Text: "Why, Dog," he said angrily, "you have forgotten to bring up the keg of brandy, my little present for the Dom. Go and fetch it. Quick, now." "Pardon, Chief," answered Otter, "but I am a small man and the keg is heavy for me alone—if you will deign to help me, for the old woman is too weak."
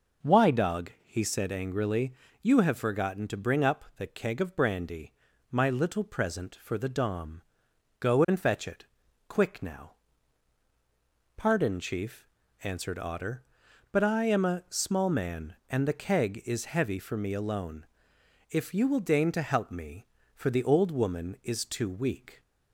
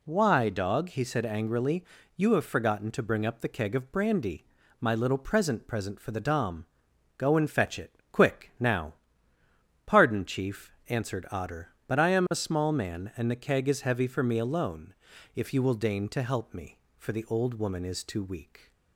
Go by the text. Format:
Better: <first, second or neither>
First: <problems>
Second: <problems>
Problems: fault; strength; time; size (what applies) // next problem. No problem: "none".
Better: first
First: none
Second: says "present" twice; at 5.6 s